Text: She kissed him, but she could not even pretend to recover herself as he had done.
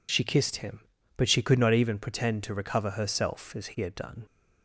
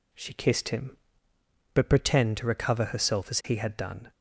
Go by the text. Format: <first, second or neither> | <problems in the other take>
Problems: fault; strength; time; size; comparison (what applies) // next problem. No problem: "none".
first | skips "she could not even"; at 1.8 s